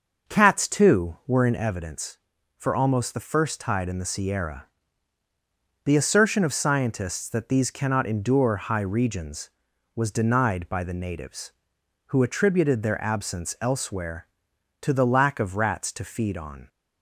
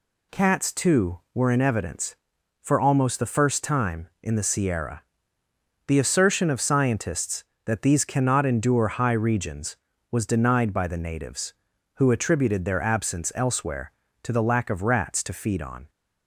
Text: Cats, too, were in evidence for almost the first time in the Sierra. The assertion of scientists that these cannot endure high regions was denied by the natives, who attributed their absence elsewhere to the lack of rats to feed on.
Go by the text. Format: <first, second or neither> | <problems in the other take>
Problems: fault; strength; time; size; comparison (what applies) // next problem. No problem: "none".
second | starts louder than the rest; until 1.3 s; 6.5 dB // says "tide" for "time"; at 3.6 s